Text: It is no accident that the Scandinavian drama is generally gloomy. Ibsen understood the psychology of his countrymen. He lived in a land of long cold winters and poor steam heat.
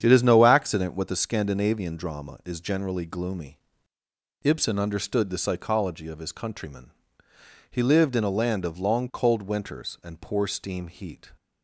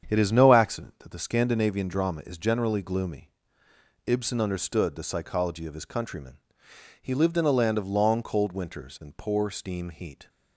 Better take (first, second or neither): second